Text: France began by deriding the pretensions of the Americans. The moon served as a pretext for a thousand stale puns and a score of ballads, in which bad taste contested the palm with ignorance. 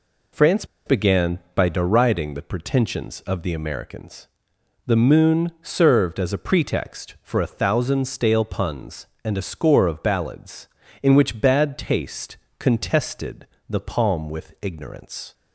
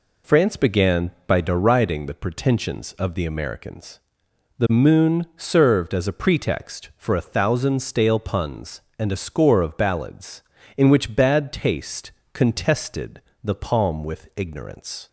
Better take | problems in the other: second | pauses between "France" and "began"; slight; at 0.6 s; 0.22 s long // pauses between "taste" and "contested"; slight; at 12.3 s; 0.22 s long; slight in the second // pauses between "contested" and "the"; slight; at 13.4 s; 0.20 s long; slight in the second

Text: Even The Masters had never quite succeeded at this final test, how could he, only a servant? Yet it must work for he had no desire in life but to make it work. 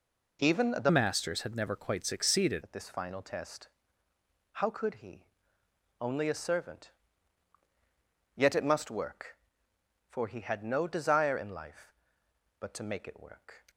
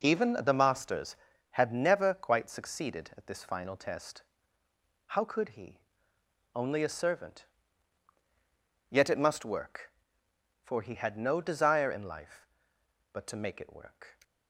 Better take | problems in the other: second | changes voice from "Masters" to "succeeded"; from 0.8 to 2.6 s; 1.8 s long

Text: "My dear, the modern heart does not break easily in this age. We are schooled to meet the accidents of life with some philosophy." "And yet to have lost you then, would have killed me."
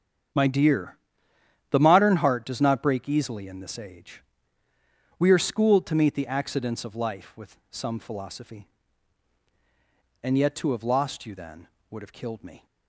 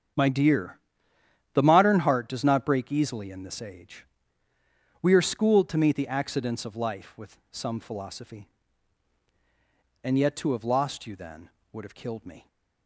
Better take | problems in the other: neither | starts louder than the rest; strong; the same in both

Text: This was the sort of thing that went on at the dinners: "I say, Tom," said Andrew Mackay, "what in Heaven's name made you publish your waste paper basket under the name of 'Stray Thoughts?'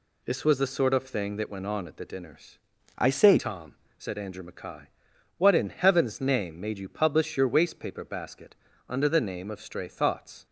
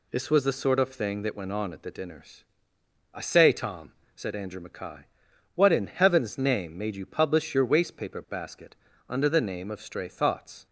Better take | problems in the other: second | changes voice from "I" to "say"; from 2.9 to 3.3 s; 0.4 s long // pauses between "basket" and "under"; slight; at 8.5 s; 0.32 s long; slight in the second

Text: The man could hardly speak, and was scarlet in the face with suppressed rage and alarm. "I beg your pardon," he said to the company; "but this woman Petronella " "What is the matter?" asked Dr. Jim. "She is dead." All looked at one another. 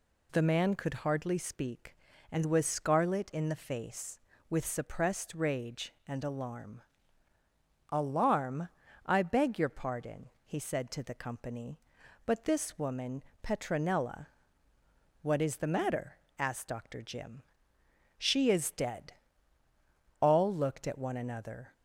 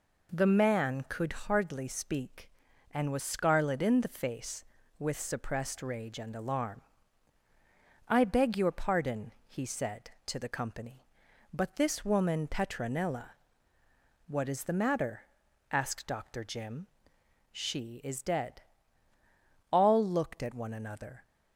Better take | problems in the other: second | says "alarm" twice; at 7.8 s // pauses between "woman" and "Petronella"; slight; at 13.2 s; 0.18 s long

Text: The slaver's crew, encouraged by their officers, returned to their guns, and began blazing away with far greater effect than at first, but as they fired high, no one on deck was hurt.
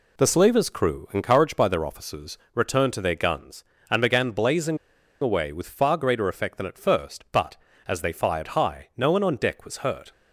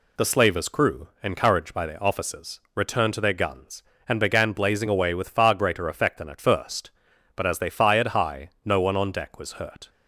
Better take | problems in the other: second | pauses between "blazing" and "away"; at 4.7 s; 0.44 s long

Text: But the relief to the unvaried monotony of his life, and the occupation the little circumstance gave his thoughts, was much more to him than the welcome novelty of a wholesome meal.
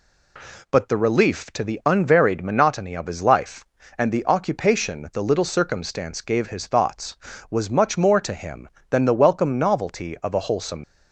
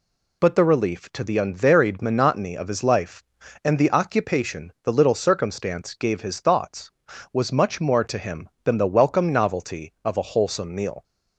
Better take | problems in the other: second | stops before "meal"; at 10.8 s

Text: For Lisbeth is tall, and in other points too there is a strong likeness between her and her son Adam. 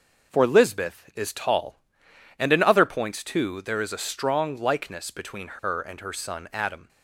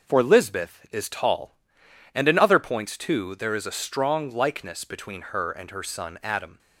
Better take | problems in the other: neither | none

